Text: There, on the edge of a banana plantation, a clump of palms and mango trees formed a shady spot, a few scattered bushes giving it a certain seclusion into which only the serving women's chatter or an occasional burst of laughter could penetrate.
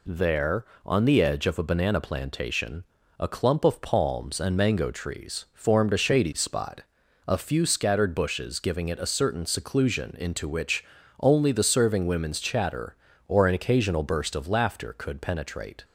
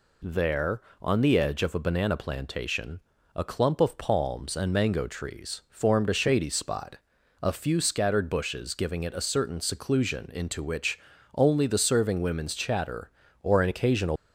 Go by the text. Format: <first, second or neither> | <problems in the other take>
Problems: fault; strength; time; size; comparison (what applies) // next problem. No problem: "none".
first | pauses between "which" and "only"; at 10.9 s; 0.38 s long; also in the first // stops before "burst of laughter could penetrate"; at 14.1 s